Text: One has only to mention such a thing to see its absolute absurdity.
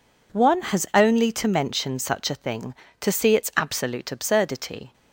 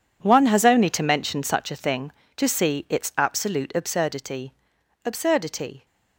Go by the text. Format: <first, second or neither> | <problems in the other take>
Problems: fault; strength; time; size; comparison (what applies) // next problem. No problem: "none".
first | says "absurdity" twice; at 5.0 s